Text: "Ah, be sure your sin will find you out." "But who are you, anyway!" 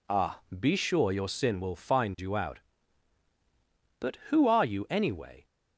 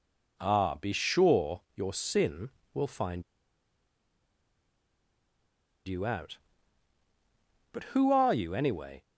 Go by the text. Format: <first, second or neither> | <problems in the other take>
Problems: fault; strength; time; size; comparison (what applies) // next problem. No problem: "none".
first | pauses between "find" and "you"; strong; at 3.2 s; 2.6 s long